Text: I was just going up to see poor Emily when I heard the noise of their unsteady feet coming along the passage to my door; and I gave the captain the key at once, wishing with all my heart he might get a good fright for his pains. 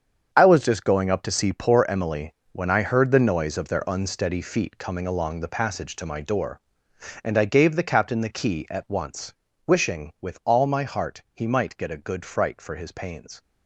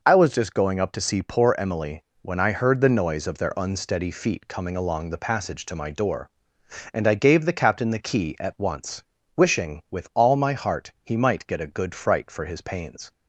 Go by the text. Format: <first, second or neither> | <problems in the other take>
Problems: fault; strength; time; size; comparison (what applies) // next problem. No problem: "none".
second | gets quieter; strong; throughout; 11.5 dB // pauses between "Emily" and "when"; slight; at 2.3 s; 0.22 s long; slight in the second